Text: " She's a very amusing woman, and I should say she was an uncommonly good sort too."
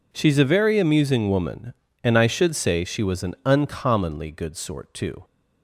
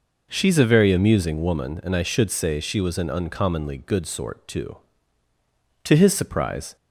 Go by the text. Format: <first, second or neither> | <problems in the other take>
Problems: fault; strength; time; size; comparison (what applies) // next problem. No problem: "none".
first | goes on to say "To his surprise"; noticeable; from 5.8 s on; 0.90 s long